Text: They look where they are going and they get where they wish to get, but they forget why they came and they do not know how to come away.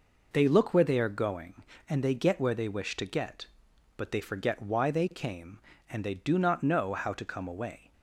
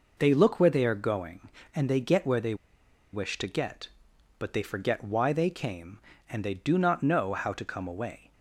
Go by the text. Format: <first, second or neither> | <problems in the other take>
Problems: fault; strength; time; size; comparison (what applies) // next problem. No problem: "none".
first | pauses between "they" and "wish"; noticeable; at 2.5 s; 0.58 s long